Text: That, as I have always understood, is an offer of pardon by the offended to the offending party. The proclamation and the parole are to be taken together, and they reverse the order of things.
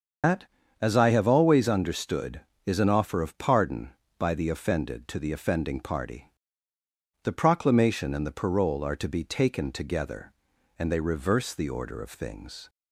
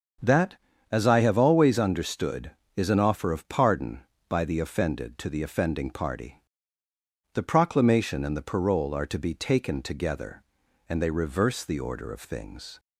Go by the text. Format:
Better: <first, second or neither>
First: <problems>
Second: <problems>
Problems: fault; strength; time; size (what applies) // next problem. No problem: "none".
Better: second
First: loses the start of "That"; at 0.2 s; 155 ms // starts louder than the rest; until 1.6 s; 7 dB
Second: starts louder than the rest; until 1.5 s; 7 dB